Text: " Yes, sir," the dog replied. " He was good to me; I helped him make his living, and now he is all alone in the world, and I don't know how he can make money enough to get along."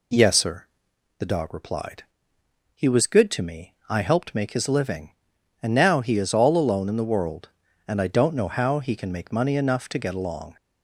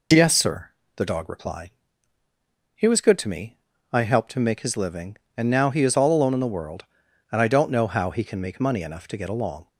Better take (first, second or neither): second